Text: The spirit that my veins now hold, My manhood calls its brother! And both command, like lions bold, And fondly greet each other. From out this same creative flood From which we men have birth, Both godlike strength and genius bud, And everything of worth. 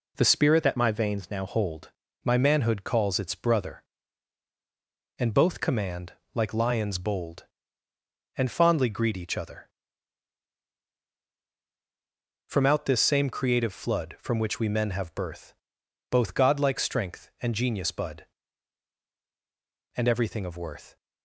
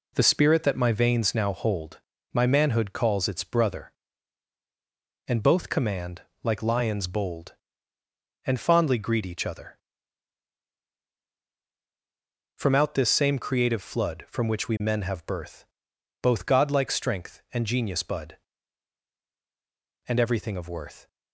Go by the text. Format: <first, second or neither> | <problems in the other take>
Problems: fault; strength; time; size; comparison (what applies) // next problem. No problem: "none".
second | changes voice from "that" to "now"; from 0.6 to 1.4 s; 0.8 s long